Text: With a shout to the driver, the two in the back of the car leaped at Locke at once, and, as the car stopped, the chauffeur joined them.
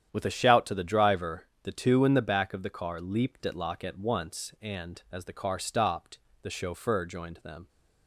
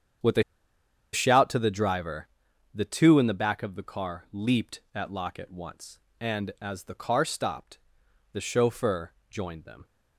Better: first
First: starts louder than the rest; strong; until 1.1 s; 9.5 dB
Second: starts louder than the rest; strong; until 1.9 s; 8.5 dB // pauses between "a" and "shout"; noticeable; at 0.4 s; 0.70 s long // pauses between "chauffeur" and "joined"; slight; at 9.1 s; 0.16 s long

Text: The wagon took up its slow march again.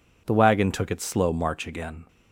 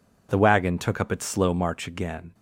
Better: second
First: skips "up"; at 0.8 s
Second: none

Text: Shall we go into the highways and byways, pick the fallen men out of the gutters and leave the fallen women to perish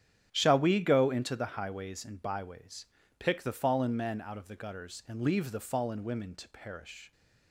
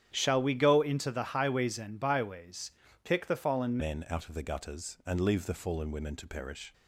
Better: first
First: starts louder than the rest; strong; until 1.3 s; 9.5 dB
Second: starts louder than the rest; strong; until 1.1 s; 9.5 dB // changes voice at "men"; from 3.7 s on; 3.0 s long

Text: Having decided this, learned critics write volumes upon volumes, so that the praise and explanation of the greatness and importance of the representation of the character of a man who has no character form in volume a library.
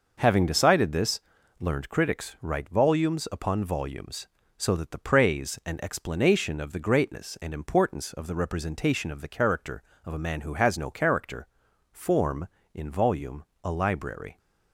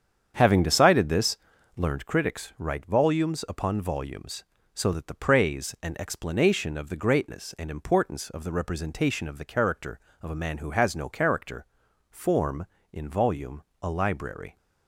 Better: first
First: pauses between "character" and "form"; noticeable; at 11.4 s; 0.46 s long // pauses between "volume" and "a"; slight; at 13.4 s; 0.18 s long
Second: starts louder than the rest; strong; until 2.1 s; 8 dB // pauses between "character" and "form"; noticeable; at 11.6 s; 0.46 s long // pauses between "volume" and "a"; slight; at 13.6 s; 0.18 s long

